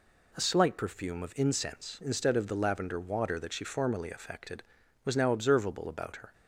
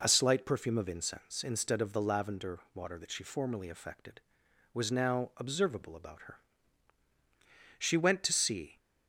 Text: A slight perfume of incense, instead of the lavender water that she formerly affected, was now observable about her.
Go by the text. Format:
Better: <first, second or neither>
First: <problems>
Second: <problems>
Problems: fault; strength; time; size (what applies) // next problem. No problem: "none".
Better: first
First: none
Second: pauses between "lavender" and "water"; slight; at 2.5 s; 0.16 s long // goes on to say "She went to see"; noticeable; from 7.7 s on; 0.98 s long